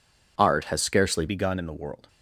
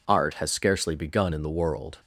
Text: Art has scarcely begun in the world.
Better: second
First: changes voice at "begun"; from 1.2 s on; 0.8 s long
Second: none

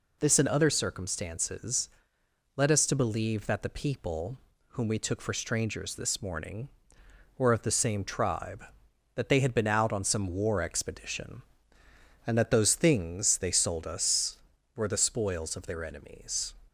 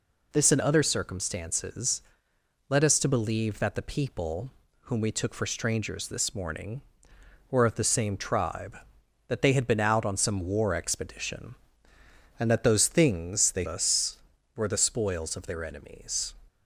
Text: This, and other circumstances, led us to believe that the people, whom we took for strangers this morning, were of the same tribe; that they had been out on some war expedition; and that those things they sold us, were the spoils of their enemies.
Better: first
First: none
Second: skips "sold"; at 13.6 s

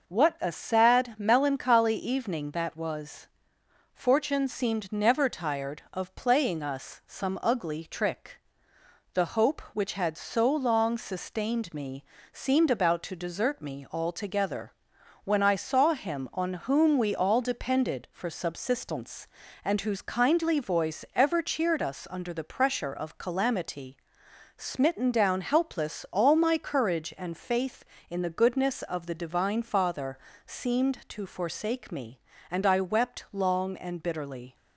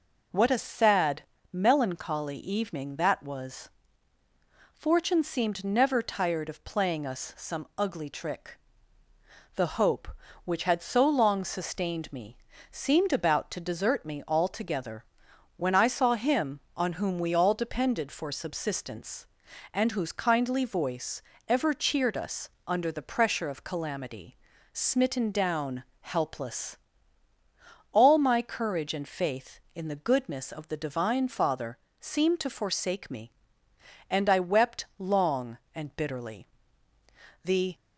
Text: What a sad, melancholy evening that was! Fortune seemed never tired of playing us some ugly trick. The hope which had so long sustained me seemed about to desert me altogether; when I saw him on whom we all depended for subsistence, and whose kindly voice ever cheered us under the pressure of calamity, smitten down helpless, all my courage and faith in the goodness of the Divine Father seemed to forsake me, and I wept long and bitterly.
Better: first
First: pauses between "me" and "seemed"; slight; at 12.0 s; 0.28 s long // pauses between "Father" and "seemed"; slight; at 30.1 s; 0.28 s long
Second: pauses between "me" and "seemed"; slight; at 12.3 s; 0.34 s long // pauses between "voice" and "ever"; slight; at 21.2 s; 0.28 s long // pauses between "us" and "under"; slight; at 22.4 s; 0.20 s long // pauses between "down" and "helpless"; slight; at 25.8 s; 0.20 s long // pauses between "Father" and "seemed"; slight; at 31.7 s; 0.22 s long // goes on to say "The"; slight; from 37.4 s on; 0.30 s long

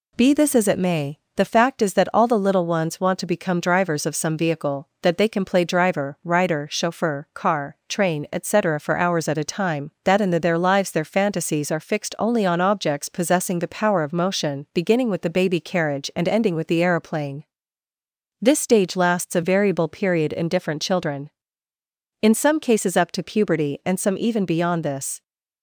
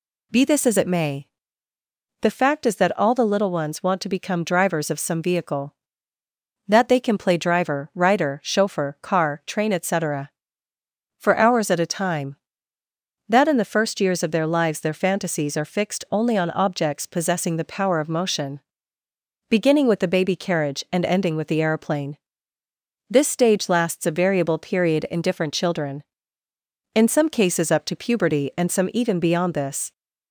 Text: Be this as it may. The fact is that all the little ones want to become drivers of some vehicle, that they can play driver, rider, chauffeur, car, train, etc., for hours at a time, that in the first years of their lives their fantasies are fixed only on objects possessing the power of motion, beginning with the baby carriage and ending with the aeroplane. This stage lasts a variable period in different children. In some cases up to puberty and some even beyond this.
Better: second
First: skips "first years of"; at 10.3 s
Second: none

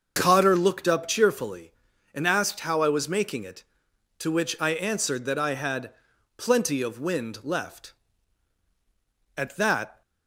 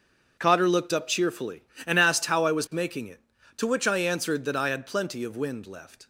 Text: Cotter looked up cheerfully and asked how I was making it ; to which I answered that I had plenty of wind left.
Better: second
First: starts louder than the rest; until 1.1 s; 6.5 dB // pauses between "had" and "plenty"; noticeable; at 5.9 s; 0.46 s long // goes on to say "At that"; noticeable; from 9.3 s on; 0.66 s long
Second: starts louder than the rest; until 1.4 s; 6.5 dB

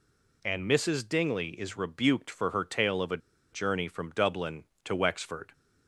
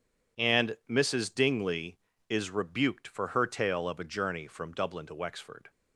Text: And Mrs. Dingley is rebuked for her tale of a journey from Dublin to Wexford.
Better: second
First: pauses between "a" and "journey"; slight; at 3.1 s; 0.34 s long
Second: none

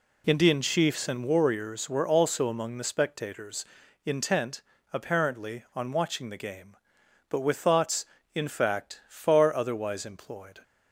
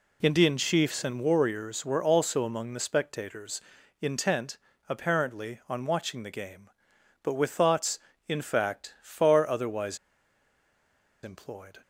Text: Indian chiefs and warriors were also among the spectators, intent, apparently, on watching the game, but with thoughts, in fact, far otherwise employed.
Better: first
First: none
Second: pauses between "otherwise" and "employed"; strong; at 9.9 s; 1.2 s long

